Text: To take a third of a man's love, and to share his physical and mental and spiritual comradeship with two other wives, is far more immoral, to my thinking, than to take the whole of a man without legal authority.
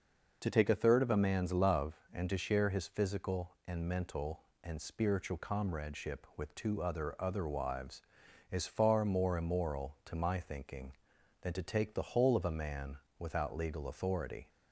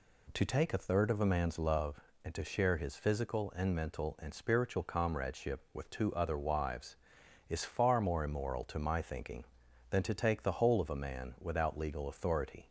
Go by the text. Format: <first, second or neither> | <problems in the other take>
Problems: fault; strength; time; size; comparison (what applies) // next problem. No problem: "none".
second | says "other" twice; at 7.1 s // pauses between "man" and "without"; slight; at 12.9 s; 0.20 s long